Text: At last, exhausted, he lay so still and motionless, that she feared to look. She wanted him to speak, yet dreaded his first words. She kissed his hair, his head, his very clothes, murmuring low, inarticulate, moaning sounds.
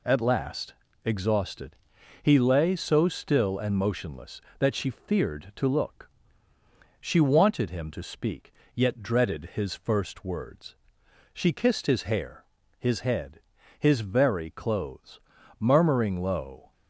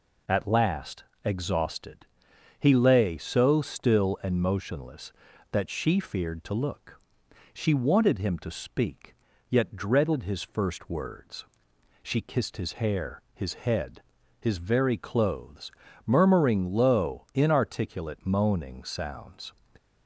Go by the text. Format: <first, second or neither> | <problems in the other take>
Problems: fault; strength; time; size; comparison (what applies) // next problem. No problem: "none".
second | stops before "inarticulate moaning sounds"; at 16.7 s